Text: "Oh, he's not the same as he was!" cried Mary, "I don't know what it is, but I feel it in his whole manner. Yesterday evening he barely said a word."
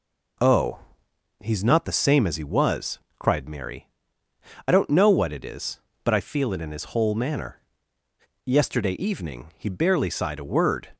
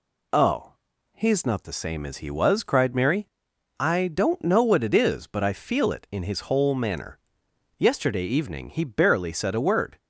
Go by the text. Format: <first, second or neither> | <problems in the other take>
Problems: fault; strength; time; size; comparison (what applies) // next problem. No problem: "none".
second | says "sighed" for "said"; at 10.1 s